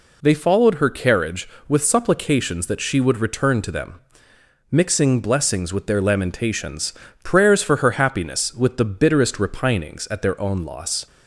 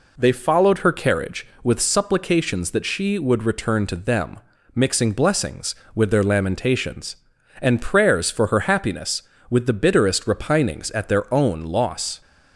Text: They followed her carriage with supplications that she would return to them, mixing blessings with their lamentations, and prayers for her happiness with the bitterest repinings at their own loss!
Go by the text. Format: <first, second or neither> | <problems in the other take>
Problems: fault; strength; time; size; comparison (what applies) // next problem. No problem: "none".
second | skips "and"; at 7.0 s